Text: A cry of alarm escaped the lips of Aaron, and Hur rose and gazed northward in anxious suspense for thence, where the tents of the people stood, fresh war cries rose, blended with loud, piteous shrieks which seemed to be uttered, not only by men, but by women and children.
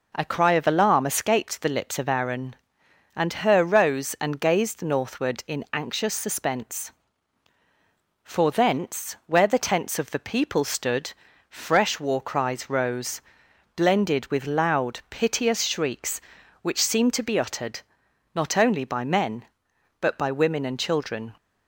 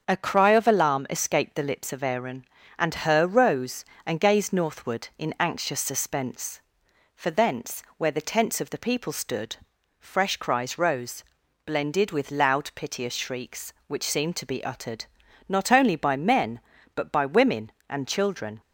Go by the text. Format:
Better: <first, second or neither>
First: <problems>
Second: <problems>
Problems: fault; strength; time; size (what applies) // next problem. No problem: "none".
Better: first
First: none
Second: starts louder than the rest; until 1.0 s; 7 dB // skips "war"; at 10.3 s